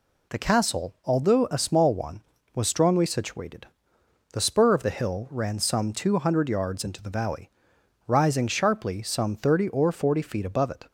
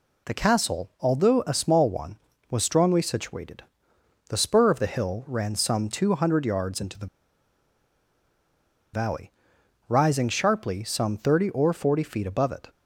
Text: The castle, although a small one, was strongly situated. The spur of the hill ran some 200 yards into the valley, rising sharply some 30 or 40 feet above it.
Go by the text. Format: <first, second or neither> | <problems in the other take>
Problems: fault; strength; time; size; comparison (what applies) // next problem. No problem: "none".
first | pauses between "the" and "valley"; strong; at 7.0 s; 1.8 s long